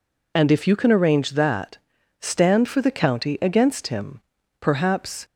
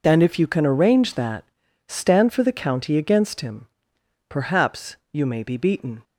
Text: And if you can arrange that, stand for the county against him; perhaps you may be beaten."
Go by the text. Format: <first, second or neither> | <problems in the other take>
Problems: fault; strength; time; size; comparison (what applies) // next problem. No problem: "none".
second | stops before "you may be beaten"; at 5.2 s